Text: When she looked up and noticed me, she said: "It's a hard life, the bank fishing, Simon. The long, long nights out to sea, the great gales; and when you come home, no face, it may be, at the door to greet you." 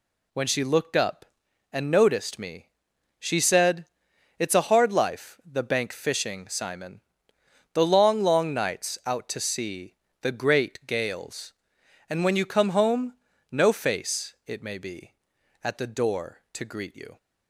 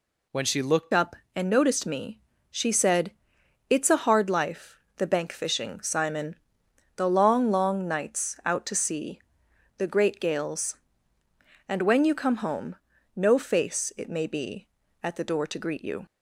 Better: first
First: none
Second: changes voice at "up"; from 0.9 s on; 15.1 s long

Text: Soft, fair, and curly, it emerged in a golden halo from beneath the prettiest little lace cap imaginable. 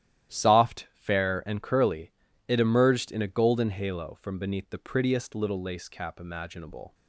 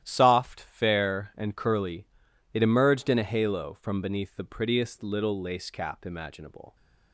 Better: first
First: starts louder than the rest; strong; until 1.3 s; 12 dB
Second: starts louder than the rest; strong; until 1.0 s; 12 dB // skips "golden"; at 3.2 s

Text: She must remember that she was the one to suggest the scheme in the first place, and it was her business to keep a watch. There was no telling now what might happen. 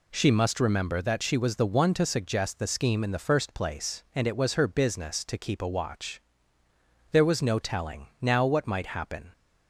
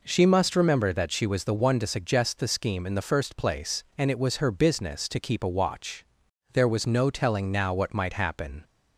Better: neither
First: none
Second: none

